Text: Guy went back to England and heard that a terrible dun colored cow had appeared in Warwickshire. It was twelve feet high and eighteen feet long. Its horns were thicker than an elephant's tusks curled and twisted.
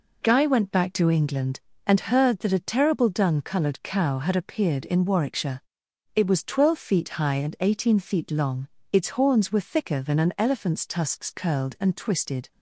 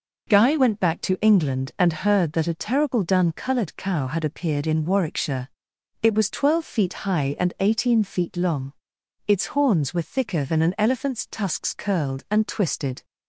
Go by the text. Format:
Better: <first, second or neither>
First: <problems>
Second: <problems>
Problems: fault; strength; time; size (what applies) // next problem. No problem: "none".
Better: neither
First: none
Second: none